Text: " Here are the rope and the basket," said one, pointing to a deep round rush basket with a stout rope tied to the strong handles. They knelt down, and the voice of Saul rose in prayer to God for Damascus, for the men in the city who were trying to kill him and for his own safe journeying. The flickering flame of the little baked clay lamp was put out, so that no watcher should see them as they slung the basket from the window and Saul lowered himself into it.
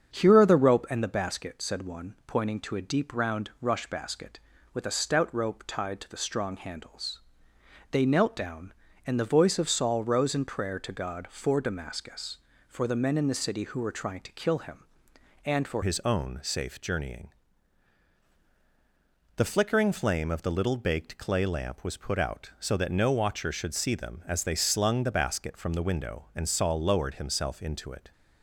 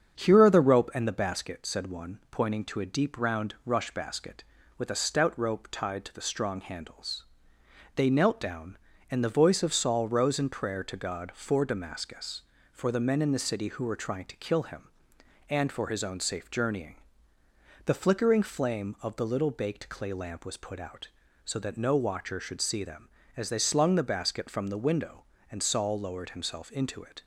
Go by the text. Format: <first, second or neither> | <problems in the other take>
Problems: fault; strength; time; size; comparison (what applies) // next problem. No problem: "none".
second | starts louder than the rest; strong; until 1.1 s; 7.5 dB; strong in the second // changes voice at "his"; from 15.8 s on; 12.3 s long